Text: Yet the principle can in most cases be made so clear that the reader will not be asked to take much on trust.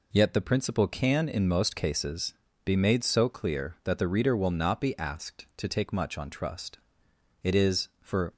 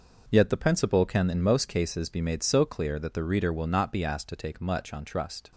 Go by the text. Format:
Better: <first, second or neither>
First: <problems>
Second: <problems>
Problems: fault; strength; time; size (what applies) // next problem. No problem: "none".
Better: second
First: pauses between "cases" and "be"; slight; at 2.3 s; 0.30 s long // goes on to say "It is for"; noticeable; from 7.4 s on; 0.92 s long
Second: none